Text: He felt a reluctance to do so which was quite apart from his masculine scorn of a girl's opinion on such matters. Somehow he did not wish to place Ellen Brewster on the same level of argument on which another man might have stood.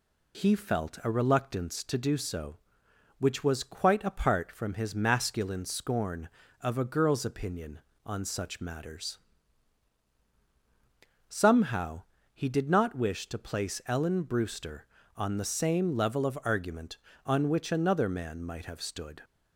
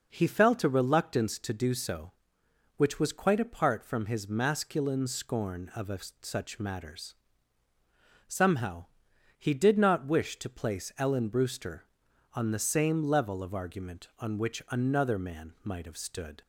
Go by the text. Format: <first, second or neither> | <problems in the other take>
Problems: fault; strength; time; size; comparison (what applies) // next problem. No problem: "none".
first | skips "girl's opinion on"; at 6.1 s // pauses between "Somehow" and "he"; noticeable; at 8.8 s; 0.52 s long; slight in the first